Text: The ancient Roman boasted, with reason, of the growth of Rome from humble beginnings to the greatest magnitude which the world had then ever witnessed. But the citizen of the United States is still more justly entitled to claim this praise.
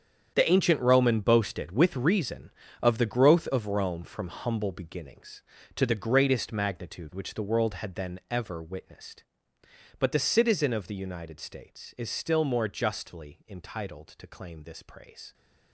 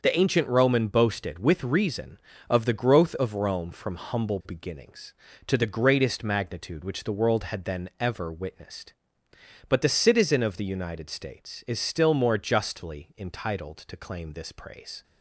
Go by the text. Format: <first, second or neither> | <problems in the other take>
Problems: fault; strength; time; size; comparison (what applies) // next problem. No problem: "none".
second | gets quieter; strong; throughout; 13 dB // starts louder than the rest; strong; until 1.3 s; 8 dB; also in the second